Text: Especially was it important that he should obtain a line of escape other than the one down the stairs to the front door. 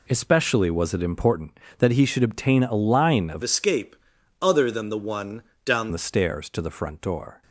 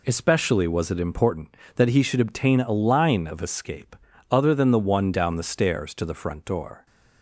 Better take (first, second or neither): second